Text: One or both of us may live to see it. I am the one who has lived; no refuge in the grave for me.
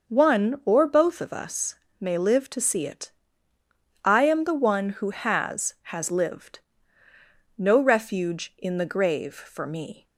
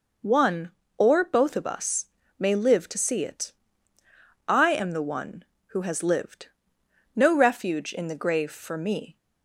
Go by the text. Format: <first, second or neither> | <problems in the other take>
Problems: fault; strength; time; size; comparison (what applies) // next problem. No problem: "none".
second | starts louder than the rest; noticeable; until 1.1 s; 6 dB // pauses between "us" and "may"; slight; at 1.7 s; 0.24 s long; slight in the second // says "has" twice; at 5.8 s